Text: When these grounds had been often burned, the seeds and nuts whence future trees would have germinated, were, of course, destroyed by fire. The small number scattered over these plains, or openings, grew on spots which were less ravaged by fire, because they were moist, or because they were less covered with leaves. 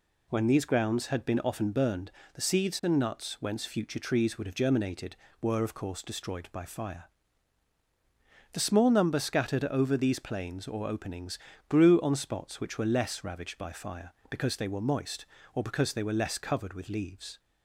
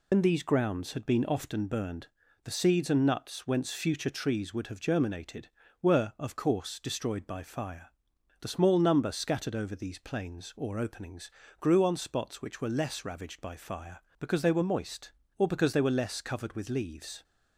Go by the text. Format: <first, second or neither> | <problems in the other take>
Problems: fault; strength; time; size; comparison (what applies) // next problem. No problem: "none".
first | loses the start of "When"; at 0.1 s; 95 ms